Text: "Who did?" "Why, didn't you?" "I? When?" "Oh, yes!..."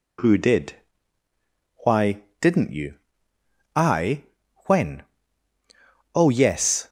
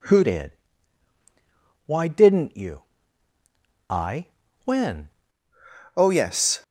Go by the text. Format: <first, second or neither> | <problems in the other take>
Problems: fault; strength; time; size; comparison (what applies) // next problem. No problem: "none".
first | changes voice from "did" to "When"; from 0.2 to 5.0 s; 4.8 s long